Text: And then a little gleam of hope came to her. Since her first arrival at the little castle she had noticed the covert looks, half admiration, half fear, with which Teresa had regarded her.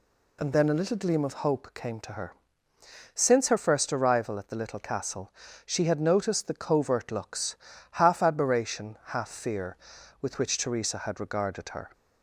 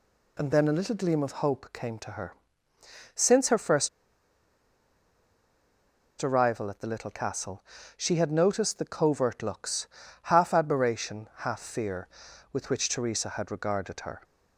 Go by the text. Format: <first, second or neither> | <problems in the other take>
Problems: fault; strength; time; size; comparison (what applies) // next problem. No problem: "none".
first | pauses between "first" and "arrival"; strong; at 3.8 s; 2.3 s long // pauses between "castle" and "she"; slight; at 7.6 s; 0.32 s long; slight in the first